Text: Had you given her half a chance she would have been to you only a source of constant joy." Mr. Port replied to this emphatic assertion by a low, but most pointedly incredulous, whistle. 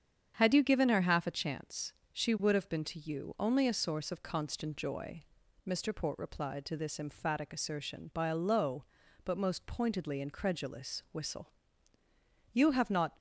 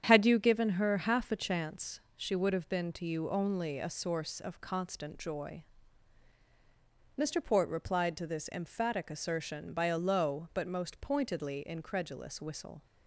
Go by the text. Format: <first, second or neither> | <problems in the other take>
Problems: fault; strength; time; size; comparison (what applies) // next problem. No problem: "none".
second | starts louder than the rest; strong; until 1.4 s; 8 dB; strong in the second // pauses between "chance" and "she"; slight; at 1.9 s; 0.18 s long; slight in the second // goes on to say "You have not"; noticeable; from 12.5 s on; 0.64 s long